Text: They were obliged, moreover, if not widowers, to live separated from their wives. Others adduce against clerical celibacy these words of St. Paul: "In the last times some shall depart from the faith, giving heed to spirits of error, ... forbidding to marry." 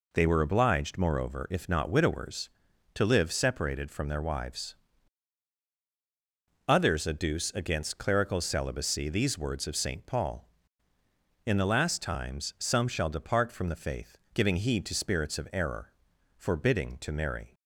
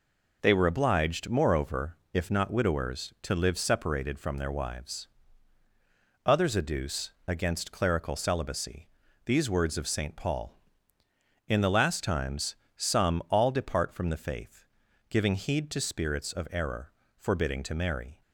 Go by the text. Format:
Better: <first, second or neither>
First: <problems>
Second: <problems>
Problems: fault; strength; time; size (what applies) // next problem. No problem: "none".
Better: first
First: none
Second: pauses between "adduce" and "against"; slight; at 7.1 s; 0.16 s long // pauses between "celibacy" and "these"; at 8.8 s; 0.38 s long // pauses between "times" and "some"; slight; at 12.5 s; 0.20 s long // says "all" for "shall"; at 13.2 s